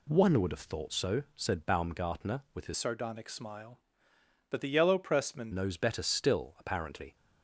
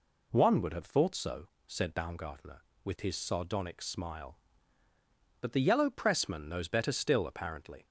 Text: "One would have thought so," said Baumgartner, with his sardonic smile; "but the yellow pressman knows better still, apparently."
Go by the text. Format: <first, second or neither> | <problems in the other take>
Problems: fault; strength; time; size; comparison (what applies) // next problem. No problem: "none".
second | changes voice from "sardonic" to "pressman"; from 2.7 to 5.5 s; 2.8 s long